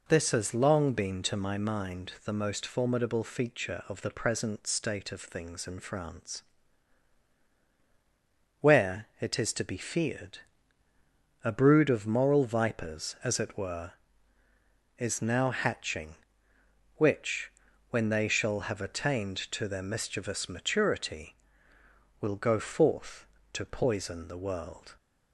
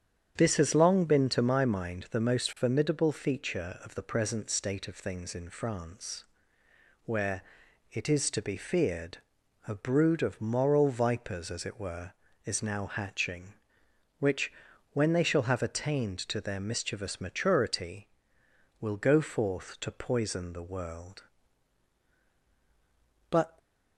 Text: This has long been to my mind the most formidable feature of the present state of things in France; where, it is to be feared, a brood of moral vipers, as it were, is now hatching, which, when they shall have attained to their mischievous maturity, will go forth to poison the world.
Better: first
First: none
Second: starts louder than the rest; strong; until 1.3 s; 8 dB // goes on to say "But"; slight; from 23.2 s on; 0.28 s long

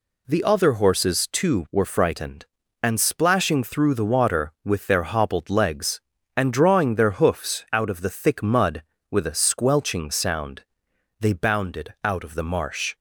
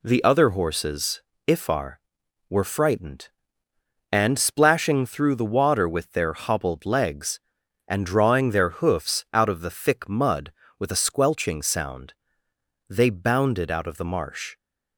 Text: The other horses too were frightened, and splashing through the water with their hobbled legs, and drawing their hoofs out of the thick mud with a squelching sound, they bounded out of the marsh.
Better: first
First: none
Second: says "ifar" for "too"; at 1.4 s

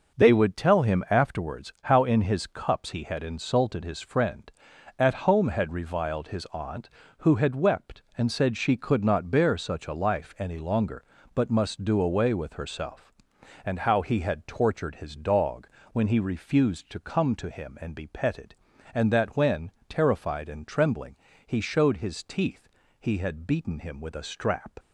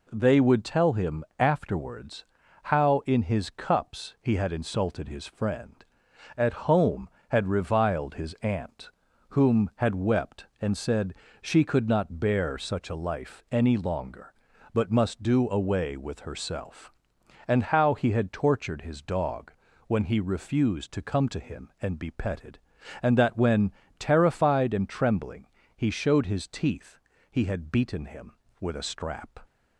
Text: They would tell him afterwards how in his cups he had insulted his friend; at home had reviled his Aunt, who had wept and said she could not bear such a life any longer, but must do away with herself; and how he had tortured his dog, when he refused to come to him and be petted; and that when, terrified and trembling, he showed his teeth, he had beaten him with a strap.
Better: first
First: none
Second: pauses between "afterwards" and "how"; at 2.2 s; 0.40 s long // says "whom" for "who"; at 9.3 s // pauses between "said" and "she"; slight; at 11.1 s; 0.30 s long

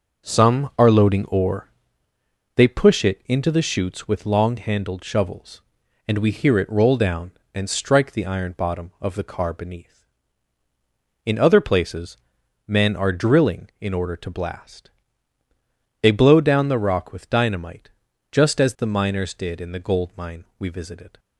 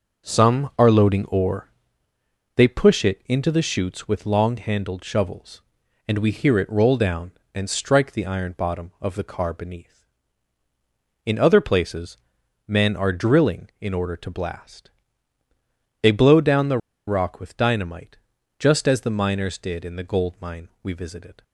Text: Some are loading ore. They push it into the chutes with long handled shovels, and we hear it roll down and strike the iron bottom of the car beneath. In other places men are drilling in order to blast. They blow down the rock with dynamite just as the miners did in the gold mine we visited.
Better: first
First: pauses between "places" and "men"; noticeable; at 12.1 s; 0.50 s long // pauses between "dynamite" and "just"; at 17.8 s; 0.42 s long // pauses between "mine" and "we"; slight; at 20.4 s; 0.16 s long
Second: pauses between "places" and "men"; noticeable; at 12.1 s; 0.50 s long // pauses between "the" and "rock"; slight; at 16.7 s; 0.29 s long // pauses between "dynamite" and "just"; at 18.1 s; 0.42 s long // pauses between "mine" and "we"; slight; at 20.6 s; 0.16 s long

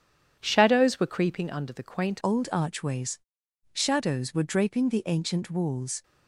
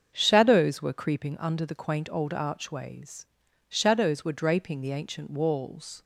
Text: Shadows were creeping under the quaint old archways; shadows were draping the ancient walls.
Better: second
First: starts louder than the rest; strong; until 1.4 s; 9 dB // changes voice at "old"; from 2.2 s on; 3.8 s long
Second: starts louder than the rest; until 1.1 s; 6.5 dB

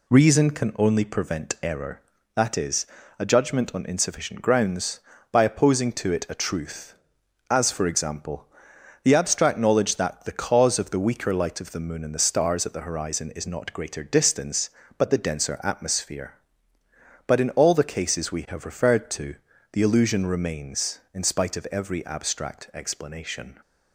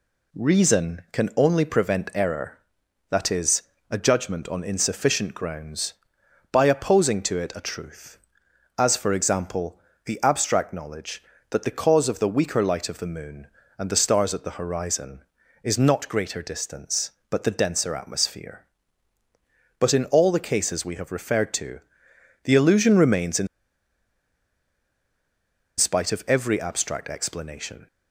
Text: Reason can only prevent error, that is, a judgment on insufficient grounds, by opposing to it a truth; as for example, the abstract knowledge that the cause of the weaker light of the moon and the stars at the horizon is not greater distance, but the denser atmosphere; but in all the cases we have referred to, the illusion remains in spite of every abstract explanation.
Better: first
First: none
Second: pauses between "in" and "spite"; strong; at 23.4 s; 2.3 s long

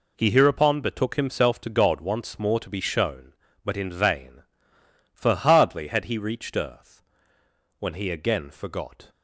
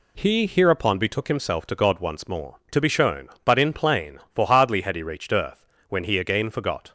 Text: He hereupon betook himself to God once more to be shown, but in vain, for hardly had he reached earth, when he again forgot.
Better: first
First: none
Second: says "plain" for "vain"; at 3.7 s

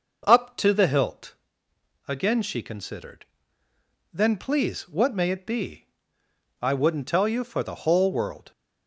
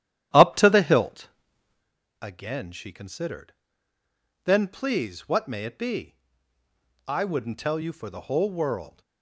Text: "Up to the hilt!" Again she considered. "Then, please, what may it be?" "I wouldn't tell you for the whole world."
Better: first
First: none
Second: starts louder than the rest; strong; until 1.9 s; 11.5 dB

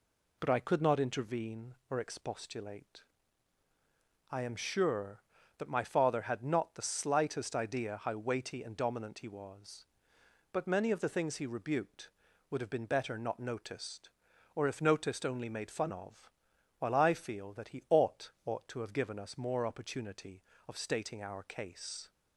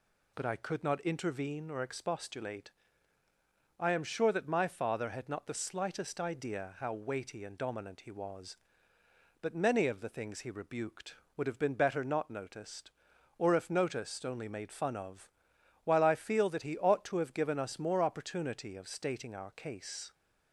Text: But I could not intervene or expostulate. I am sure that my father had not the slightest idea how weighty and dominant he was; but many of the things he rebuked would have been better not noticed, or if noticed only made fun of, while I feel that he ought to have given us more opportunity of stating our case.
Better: second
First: says "ought" twice; at 18.4 s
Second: none

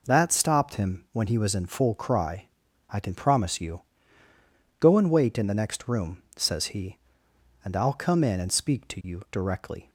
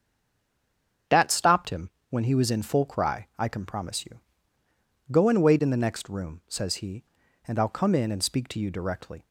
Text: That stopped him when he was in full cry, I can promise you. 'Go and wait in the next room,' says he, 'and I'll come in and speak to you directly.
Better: first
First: none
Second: stays silent before the first word; until 1.0 s; 1.0 s long // starts louder than the rest; strong; until 2.3 s; 7.5 dB // pauses between "him" and "when"; slight; at 1.8 s; 0.20 s long

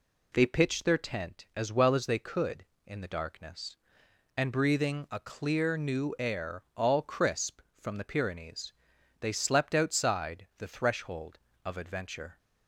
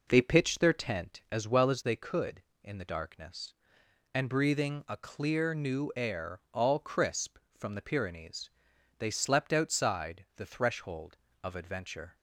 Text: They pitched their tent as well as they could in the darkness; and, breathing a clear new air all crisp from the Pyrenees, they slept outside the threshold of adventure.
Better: first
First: none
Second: starts louder than the rest; noticeable; until 1.5 s; 5 dB

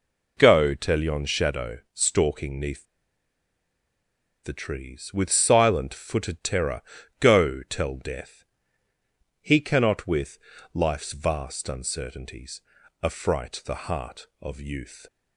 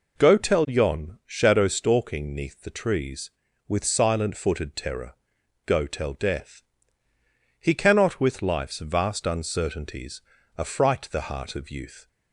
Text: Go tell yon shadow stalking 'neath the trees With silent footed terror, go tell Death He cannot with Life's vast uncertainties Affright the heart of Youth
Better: second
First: pauses between "shadow" and "stalking"; slight; at 1.7 s; 0.16 s long // pauses between "neath" and "the"; strong; at 2.8 s; 1.5 s long // pauses between "Death" and "He"; noticeable; at 8.4 s; 0.98 s long // pauses between "with" and "Life's"; slight; at 10.3 s; 0.36 s long // pauses between "uncertainties" and "Affright"; at 12.6 s; 0.40 s long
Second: pauses between "Death" and "He"; noticeable; at 6.6 s; 0.96 s long // pauses between "uncertainties" and "Affright"; slight; at 10.2 s; 0.36 s long

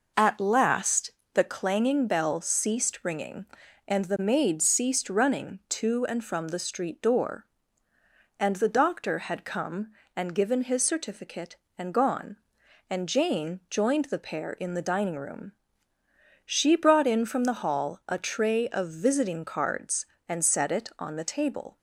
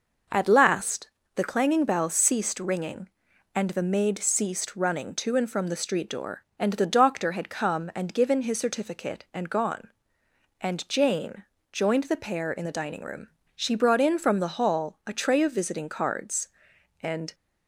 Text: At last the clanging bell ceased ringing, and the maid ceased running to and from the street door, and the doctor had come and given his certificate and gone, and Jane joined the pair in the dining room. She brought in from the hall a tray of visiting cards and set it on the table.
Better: first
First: pauses between "last" and "the"; slight; at 1.1 s; 0.22 s long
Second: pauses between "last" and "the"; slight; at 1.0 s; 0.28 s long // pauses between "Jane" and "joined"; slight; at 11.4 s; 0.28 s long // stops before "set it on the table"; at 17.3 s

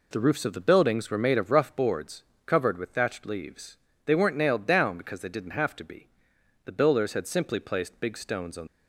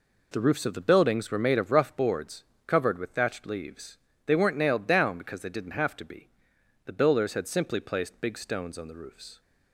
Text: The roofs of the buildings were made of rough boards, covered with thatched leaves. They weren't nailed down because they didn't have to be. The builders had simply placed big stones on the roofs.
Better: second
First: stops before "the roofs"; at 8.6 s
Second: none

